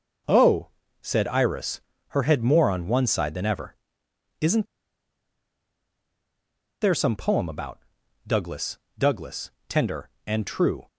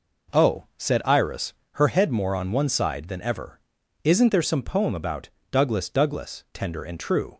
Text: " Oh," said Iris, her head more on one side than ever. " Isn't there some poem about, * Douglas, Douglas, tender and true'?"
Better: second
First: pauses between "Isn't" and "there"; strong; at 4.6 s; 2.1 s long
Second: none

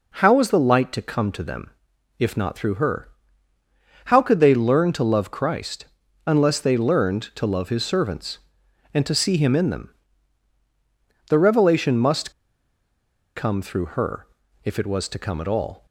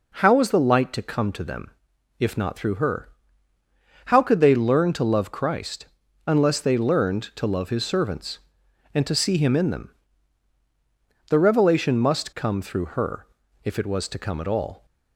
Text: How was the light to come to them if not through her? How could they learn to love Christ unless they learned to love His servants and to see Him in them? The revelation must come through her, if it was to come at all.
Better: second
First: pauses between "them" and "if"; noticeable; at 1.6 s; 0.50 s long // pauses between "Christ" and "unless"; at 5.8 s; 0.40 s long // pauses between "must" and "come"; at 12.3 s; 1.0 s long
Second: pauses between "them" and "if"; noticeable; at 1.7 s; 0.50 s long // pauses between "Christ" and "unless"; at 5.8 s; 0.40 s long

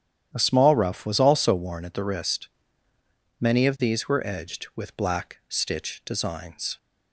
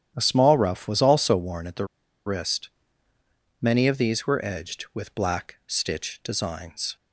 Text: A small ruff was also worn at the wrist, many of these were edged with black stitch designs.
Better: first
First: starts louder than the rest; strong; until 1.3 s; 10.5 dB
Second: starts louder than the rest; strong; until 1.1 s; 10.5 dB // pauses between "the" and "wrist"; at 1.8 s; 0.39 s long

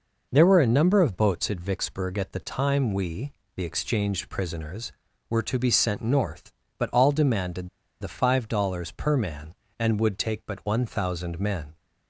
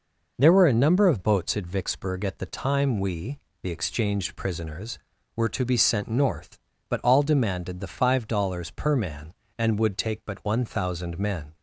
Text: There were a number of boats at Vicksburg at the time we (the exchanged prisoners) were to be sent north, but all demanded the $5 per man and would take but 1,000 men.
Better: second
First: pauses between "demanded" and "the"; slight; at 7.6 s; 0.32 s long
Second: none

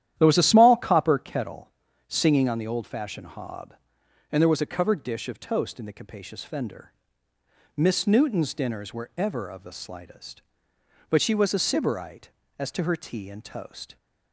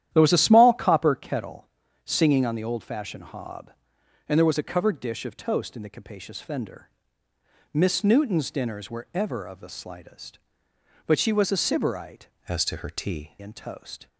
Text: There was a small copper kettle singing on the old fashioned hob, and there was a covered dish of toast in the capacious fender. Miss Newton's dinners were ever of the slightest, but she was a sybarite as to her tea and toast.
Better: first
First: starts louder than the rest; strong; until 1.1 s; 11.5 dB // pauses between "kettle" and "singing"; slight; at 1.7 s; 0.36 s long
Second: starts louder than the rest; strong; until 1.1 s; 11.5 dB // pauses between "kettle" and "singing"; slight; at 1.6 s; 0.36 s long // changes voice from "as" to "tea"; from 12.4 to 13.3 s; 0.9 s long

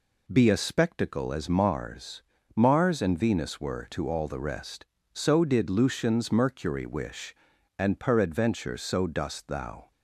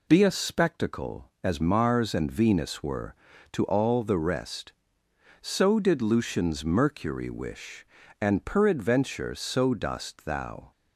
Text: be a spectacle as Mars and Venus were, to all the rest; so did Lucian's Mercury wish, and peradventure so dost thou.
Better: second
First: says "Mars" twice; at 2.5 s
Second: none

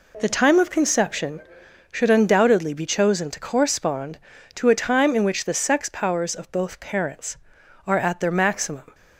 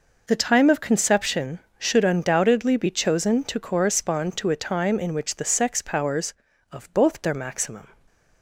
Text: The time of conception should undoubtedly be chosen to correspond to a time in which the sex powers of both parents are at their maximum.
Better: first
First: none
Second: skips "parents are at"; at 7.2 s

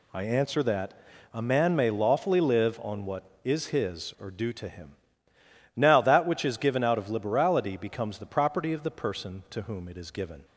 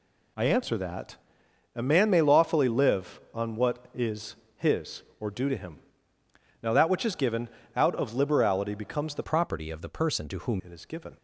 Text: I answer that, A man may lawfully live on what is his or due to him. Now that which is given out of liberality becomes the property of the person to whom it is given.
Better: first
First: none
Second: pauses between "is" and "his"; slight; at 4.3 s; 0.20 s long // pauses between "given" and "out"; slight; at 7.4 s; 0.26 s long // changes voice from "property" to "whom"; from 9.2 to 10.6 s; 1.4 s long

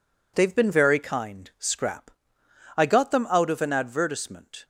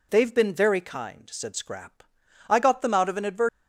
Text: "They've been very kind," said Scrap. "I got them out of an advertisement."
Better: second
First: skips "said"; at 1.5 s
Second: none

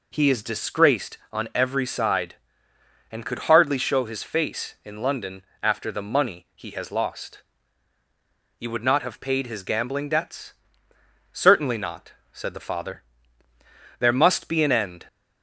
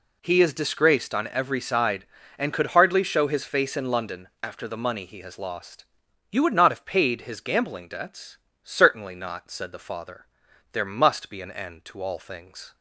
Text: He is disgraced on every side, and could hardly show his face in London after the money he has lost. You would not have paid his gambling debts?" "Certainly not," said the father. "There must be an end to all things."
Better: second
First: pauses between "London" and "after"; slight; at 5.4 s; 0.20 s long // stops before "to all things"; at 15.0 s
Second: none

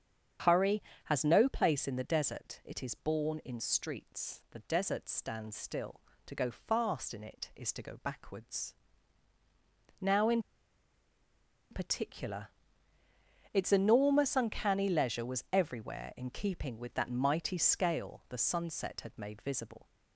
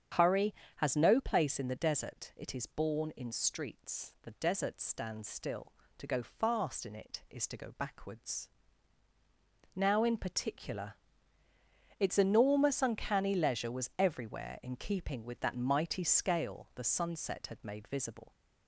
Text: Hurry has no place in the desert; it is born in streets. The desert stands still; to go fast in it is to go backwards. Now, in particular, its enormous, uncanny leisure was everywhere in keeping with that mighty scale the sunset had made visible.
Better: second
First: starts louder than the rest; strong; until 1.7 s; 8.5 dB // pauses between "in" and "particular"; strong; at 10.4 s; 1.2 s long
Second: starts louder than the rest; strong; until 1.4 s; 8.5 dB

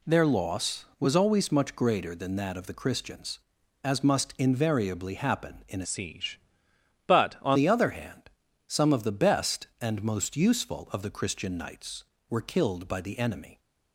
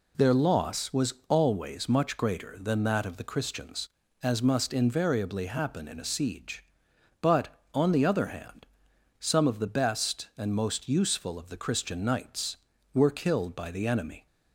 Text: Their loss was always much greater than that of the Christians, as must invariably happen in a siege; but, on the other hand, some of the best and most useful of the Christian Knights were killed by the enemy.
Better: second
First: changes voice from "siege" to "on"; from 5.8 to 7.5 s; 1.7 s long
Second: none

